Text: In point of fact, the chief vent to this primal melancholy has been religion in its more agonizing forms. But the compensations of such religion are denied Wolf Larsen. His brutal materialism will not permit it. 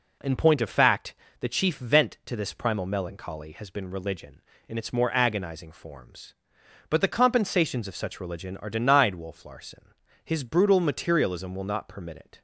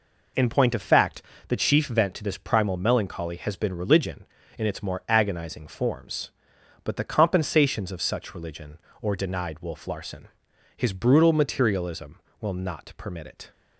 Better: first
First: none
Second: says "or" for "are"; at 9.0 s

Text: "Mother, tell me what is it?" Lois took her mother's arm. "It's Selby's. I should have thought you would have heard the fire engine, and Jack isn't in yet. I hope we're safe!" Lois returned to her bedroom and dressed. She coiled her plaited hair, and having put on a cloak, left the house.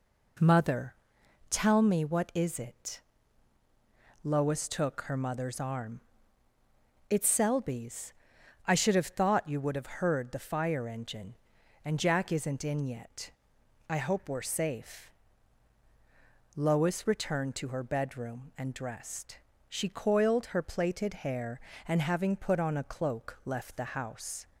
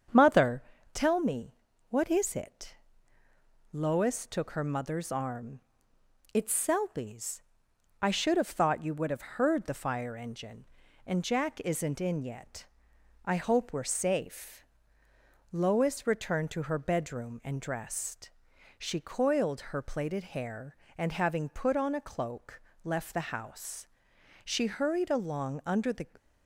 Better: first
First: none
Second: starts louder than the rest; strong; until 1.4 s; 7.5 dB // pauses between "me" and "what"; slight; at 1.5 s; 0.36 s long // goes on to say "She hurried along under the"; from 24.4 s on; 1.6 s long

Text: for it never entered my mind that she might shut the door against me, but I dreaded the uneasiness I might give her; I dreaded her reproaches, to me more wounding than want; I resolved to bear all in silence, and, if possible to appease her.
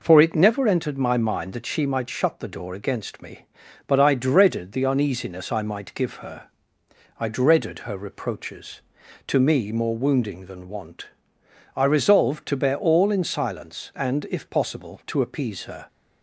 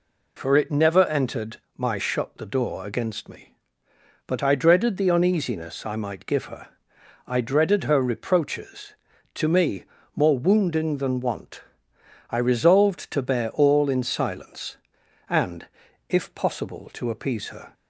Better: first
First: none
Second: pauses between "entered" and "my"; slight; at 1.5 s; 0.18 s long // skips "mind that she might"; at 1.9 s // pauses between "me" and "more"; slight; at 9.8 s; 0.30 s long

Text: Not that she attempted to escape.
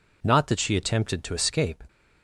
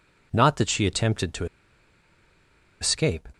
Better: first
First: none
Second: pauses between "to" and "escape"; strong; at 1.4 s; 1.3 s long

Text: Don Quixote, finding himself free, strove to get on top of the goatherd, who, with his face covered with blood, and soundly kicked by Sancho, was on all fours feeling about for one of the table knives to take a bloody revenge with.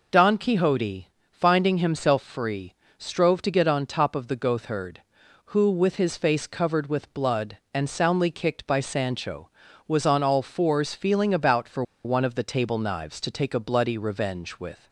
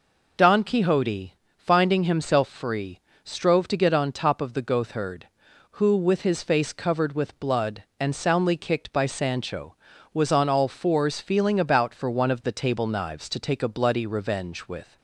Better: second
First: pauses between "for" and "one"; slight; at 11.8 s; 0.21 s long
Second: none

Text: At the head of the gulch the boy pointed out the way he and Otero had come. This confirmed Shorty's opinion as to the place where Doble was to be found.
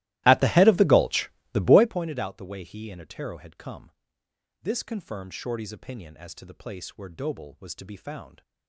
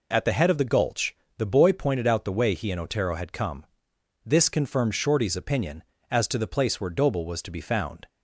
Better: second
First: starts louder than the rest; strong; until 2.0 s; 17.5 dB // pauses between "gulch" and "the"; slight; at 1.2 s; 0.22 s long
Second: pauses between "gulch" and "the"; slight; at 1.1 s; 0.22 s long

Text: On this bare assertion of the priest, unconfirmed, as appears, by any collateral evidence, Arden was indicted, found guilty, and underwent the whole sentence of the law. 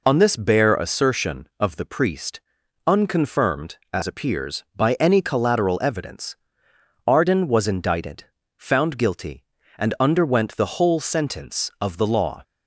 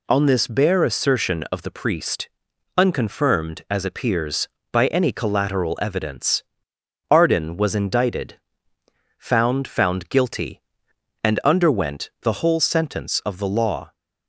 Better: first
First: none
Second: says "found" twice; at 9.6 s

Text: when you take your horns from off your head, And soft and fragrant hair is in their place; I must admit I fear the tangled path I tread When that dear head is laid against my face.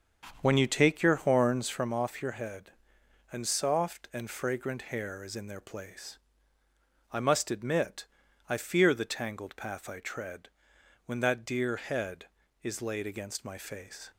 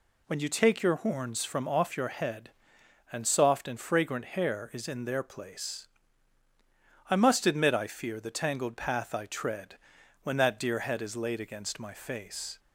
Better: second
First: starts louder than the rest; strong; until 1.9 s; 7 dB // pauses between "admit" and "I"; at 8.0 s; 0.42 s long // pauses between "tread" and "When"; noticeable; at 10.4 s; 0.56 s long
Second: pauses between "tread" and "When"; noticeable; at 9.7 s; 0.46 s long

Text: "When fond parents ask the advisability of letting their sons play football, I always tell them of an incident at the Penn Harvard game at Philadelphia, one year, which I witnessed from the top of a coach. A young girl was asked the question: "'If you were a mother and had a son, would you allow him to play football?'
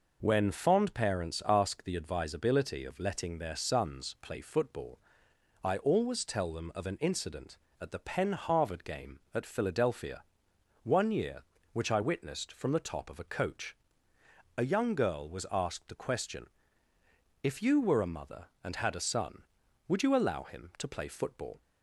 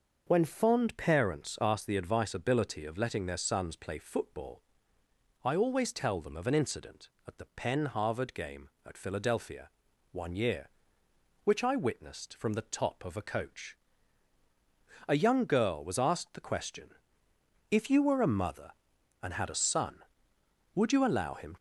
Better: first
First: none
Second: starts louder than the rest; until 1.2 s; 6 dB // stops before "to play football"; at 21.5 s

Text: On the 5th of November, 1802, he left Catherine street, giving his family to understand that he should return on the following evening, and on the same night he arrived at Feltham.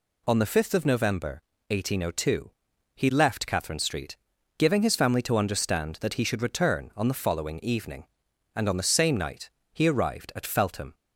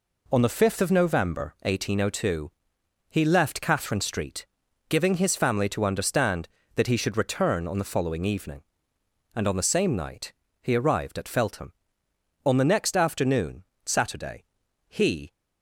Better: first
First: pauses between "night" and "he"; slight; at 9.4 s; 0.24 s long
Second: pauses between "night" and "he"; slight; at 10.3 s; 0.30 s long // goes on to say "On the next afternoon Saturday he"; strong; from 12.4 s on; 2.8 s long

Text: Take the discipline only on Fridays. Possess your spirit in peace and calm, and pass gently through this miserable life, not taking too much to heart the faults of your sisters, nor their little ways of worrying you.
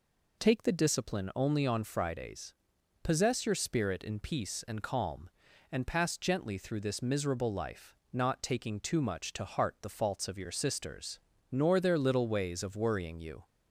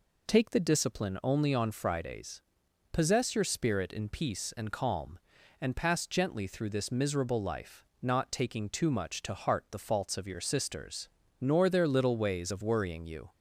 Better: neither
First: none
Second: none

